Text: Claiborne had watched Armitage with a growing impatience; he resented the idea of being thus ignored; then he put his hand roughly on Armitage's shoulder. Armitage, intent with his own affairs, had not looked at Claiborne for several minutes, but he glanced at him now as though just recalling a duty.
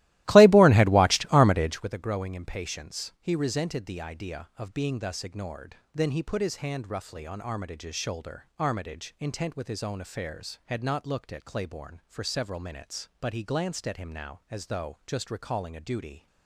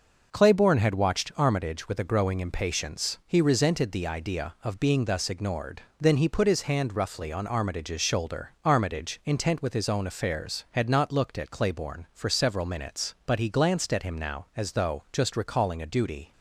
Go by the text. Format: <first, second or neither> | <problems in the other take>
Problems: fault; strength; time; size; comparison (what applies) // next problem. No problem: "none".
second | starts louder than the rest; strong; until 2.0 s; 16.5 dB